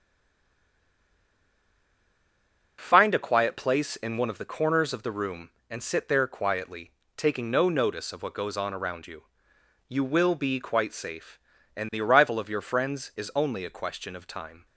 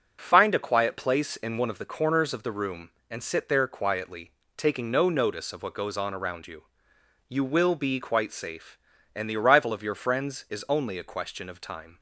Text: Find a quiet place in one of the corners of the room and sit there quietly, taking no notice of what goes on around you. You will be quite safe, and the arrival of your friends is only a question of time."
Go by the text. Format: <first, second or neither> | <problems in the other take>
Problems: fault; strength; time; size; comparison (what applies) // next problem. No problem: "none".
second | stays silent before the first word; strong; until 2.7 s; 2.7 s long